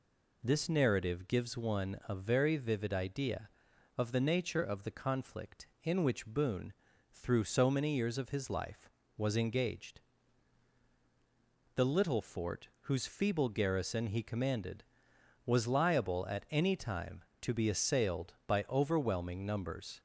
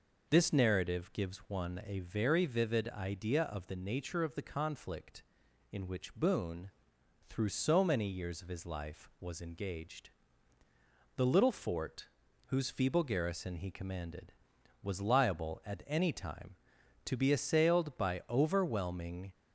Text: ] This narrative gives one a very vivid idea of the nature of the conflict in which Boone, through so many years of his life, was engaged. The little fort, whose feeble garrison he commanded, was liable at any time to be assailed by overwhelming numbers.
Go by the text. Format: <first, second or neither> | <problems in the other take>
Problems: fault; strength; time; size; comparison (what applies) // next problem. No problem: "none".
first | stops before "numbers"; at 19.3 s